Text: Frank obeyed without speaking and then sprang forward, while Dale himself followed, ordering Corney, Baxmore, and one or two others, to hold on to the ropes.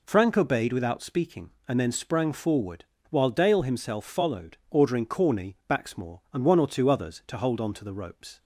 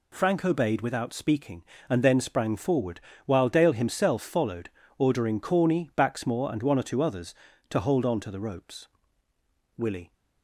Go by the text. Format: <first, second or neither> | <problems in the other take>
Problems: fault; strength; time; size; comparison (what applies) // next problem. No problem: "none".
first | goes on to say "Willie"; slight; from 9.7 s on; 0.38 s long